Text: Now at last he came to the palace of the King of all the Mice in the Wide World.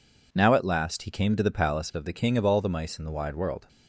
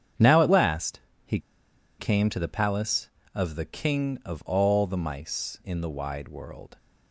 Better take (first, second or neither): first